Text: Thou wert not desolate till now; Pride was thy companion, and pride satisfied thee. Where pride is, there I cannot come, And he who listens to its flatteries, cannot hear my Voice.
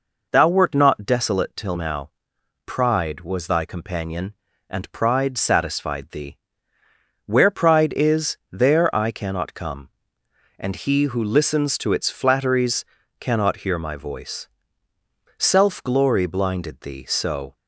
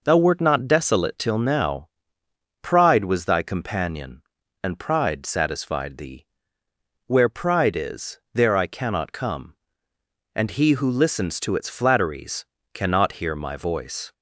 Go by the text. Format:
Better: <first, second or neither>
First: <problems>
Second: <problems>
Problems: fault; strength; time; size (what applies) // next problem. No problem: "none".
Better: second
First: goes on to say "Self glory blinded thee so"; strong; from 15.3 s on; 2.1 s long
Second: none